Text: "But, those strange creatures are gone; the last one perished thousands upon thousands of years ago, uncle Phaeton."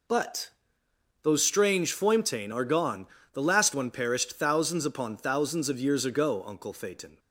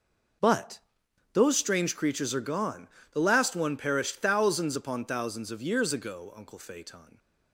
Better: second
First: says "foimtain" for "creatures"; at 1.9 s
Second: none

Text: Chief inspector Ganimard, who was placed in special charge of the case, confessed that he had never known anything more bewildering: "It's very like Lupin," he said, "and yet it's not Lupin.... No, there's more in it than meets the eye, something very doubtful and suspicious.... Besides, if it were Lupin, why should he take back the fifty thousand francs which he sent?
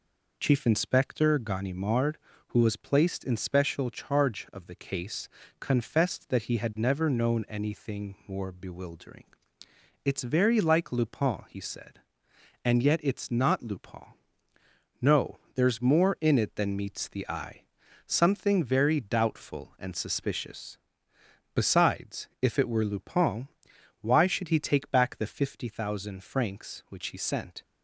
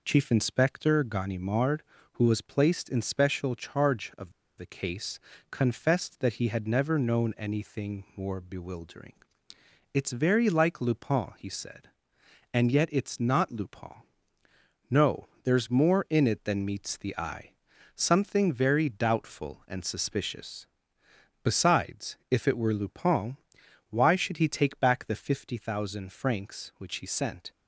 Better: first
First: none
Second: pauses between "of" and "the"; slight; at 4.3 s; 0.26 s long

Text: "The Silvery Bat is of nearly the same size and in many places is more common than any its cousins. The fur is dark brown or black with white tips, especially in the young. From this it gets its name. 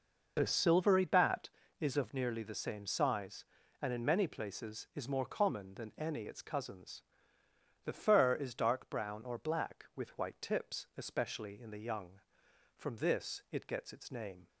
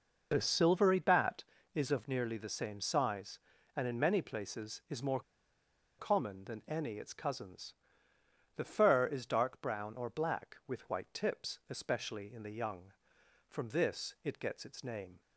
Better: first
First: none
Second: pauses between "more" and "common"; noticeable; at 5.2 s; 0.78 s long

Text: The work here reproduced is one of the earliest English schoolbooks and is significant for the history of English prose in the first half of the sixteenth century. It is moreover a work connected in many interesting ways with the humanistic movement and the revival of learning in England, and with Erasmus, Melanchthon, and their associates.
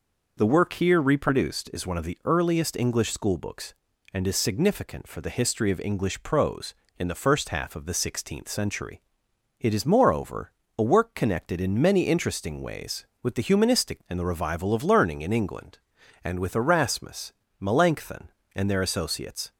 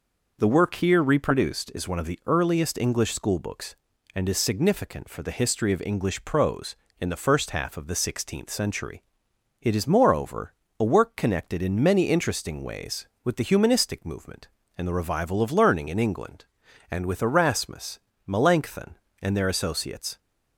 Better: second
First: pauses between "moreover" and "a"; slight; at 10.5 s; 0.26 s long // skips "movement"; at 14.0 s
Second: pauses between "moreover" and "a"; slight; at 10.5 s; 0.26 s long

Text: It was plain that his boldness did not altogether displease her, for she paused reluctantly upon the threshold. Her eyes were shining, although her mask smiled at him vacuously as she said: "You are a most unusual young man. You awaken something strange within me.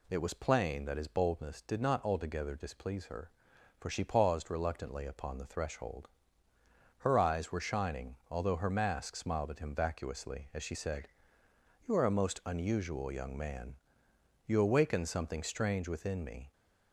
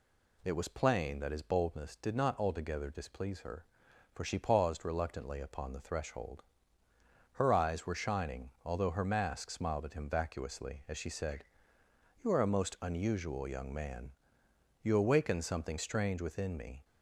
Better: neither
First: none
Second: none

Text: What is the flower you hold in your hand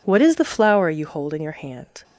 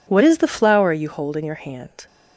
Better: neither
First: none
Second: none

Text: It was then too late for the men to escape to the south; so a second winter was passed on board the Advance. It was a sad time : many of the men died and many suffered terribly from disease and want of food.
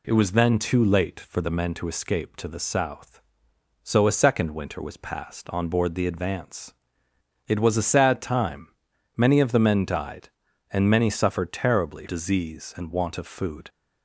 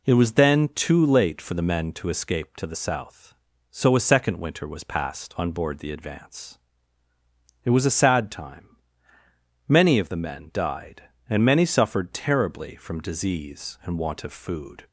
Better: second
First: skips "from"; at 12.0 s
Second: none

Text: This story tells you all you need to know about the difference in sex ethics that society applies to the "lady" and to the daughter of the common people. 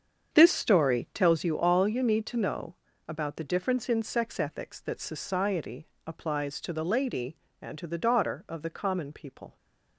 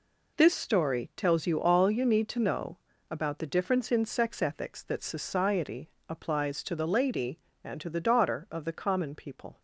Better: second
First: starts louder than the rest; strong; until 1.5 s; 7.5 dB // pauses between "know" and "about"; slight; at 2.7 s; 0.30 s long // pauses between "society" and "applies"; slight; at 5.8 s; 0.20 s long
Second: pauses between "know" and "about"; slight; at 2.7 s; 0.30 s long // pauses between "society" and "applies"; slight; at 5.8 s; 0.20 s long

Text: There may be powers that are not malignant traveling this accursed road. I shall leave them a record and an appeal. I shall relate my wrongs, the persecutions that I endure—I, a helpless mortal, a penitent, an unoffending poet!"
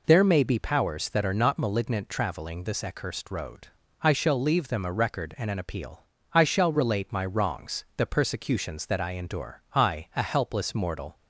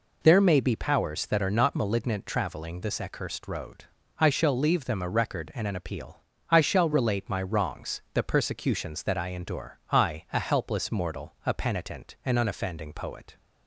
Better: second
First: stops before "a penitent an unoffending poet"; at 11.1 s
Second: none

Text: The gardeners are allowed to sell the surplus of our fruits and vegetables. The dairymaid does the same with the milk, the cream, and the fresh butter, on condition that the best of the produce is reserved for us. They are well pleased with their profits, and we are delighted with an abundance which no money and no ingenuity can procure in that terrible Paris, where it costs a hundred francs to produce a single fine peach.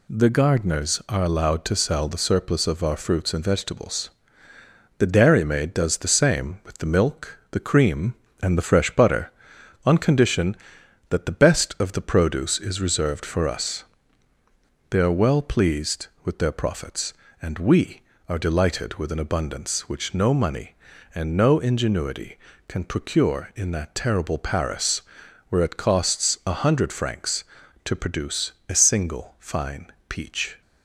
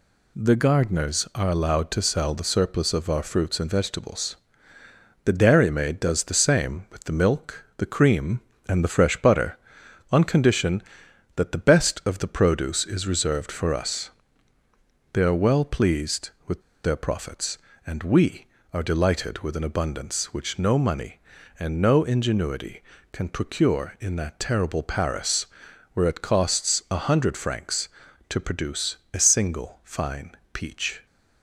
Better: first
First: pauses between "produce" and "a"; slight; at 28.5 s; 0.18 s long // pauses between "fine" and "peach"; slight; at 29.8 s; 0.22 s long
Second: pauses between "with" and "their"; slight; at 16.6 s; 0.22 s long // pauses between "produce" and "a"; slight; at 28.9 s; 0.18 s long // pauses between "fine" and "peach"; slight; at 30.3 s; 0.22 s long

